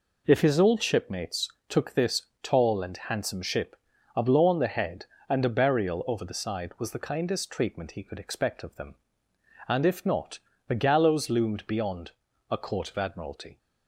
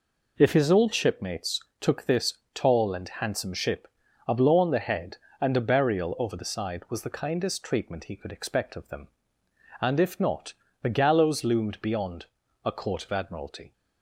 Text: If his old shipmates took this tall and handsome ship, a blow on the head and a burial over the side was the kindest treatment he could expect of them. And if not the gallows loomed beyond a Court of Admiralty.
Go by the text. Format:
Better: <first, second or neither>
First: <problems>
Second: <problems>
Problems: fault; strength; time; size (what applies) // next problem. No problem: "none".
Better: neither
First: pauses between "shipmates" and "took"; slight; at 1.4 s; 0.22 s long // pauses between "this" and "tall"; slight; at 2.2 s; 0.18 s long // pauses between "not" and "the"; slight; at 10.3 s; 0.30 s long // pauses between "beyond" and "a"; at 12.1 s; 0.38 s long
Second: pauses between "shipmates" and "took"; slight; at 1.5 s; 0.22 s long // pauses between "this" and "tall"; slight; at 2.3 s; 0.18 s long // pauses between "not" and "the"; slight; at 10.5 s; 0.30 s long // pauses between "beyond" and "a"; at 12.2 s; 0.38 s long